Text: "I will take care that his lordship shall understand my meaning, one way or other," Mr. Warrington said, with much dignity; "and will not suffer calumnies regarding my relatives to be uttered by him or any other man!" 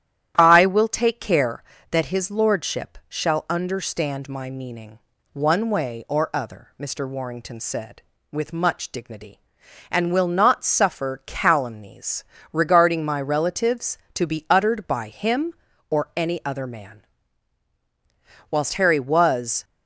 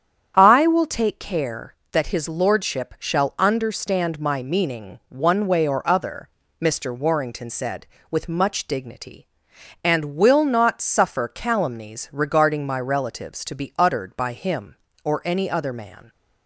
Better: second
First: starts louder than the rest; strong; until 1.3 s; 11 dB // pauses between "calumnies" and "regarding"; slight; at 12.2 s; 0.28 s long // goes on to say "Whilst Harry was"; noticeable; from 18.5 s on; 1.1 s long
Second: starts louder than the rest; strong; until 1.3 s; 9 dB

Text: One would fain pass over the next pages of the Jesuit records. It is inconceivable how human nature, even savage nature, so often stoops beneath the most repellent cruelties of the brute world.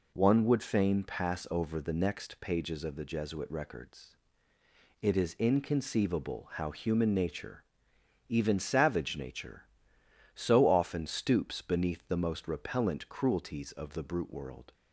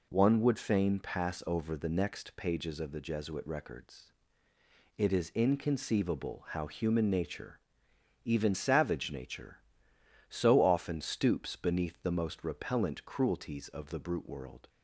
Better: neither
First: none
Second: none

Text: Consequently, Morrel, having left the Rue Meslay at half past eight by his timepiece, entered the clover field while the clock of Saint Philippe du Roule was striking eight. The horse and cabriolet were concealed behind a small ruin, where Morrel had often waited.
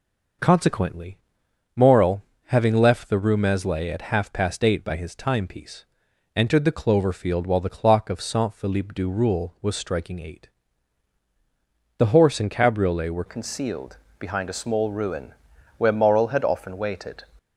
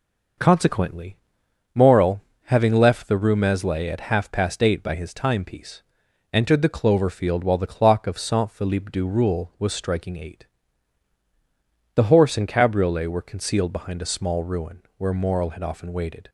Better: second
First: changes voice at "concealed"; from 13.2 s on; 4.0 s long // pauses between "concealed" and "behind"; slight; at 13.9 s; 0.24 s long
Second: none

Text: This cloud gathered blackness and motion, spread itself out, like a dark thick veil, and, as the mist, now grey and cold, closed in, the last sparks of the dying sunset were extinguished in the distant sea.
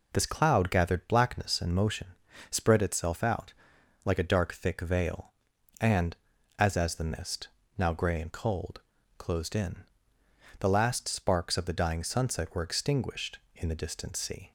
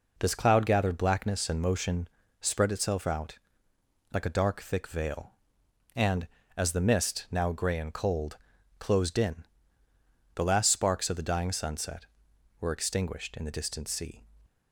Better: second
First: says "as" twice; at 6.7 s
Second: none

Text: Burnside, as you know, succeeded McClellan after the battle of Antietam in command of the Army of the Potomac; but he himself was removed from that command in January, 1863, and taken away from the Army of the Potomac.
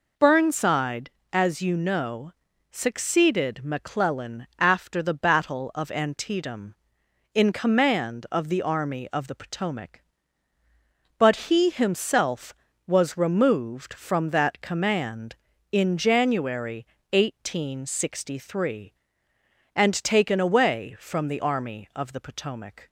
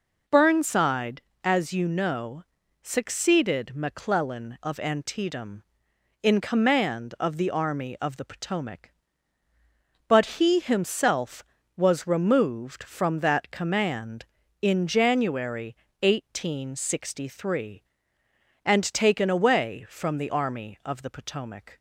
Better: first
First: none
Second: skips "after the battle"; at 4.6 s

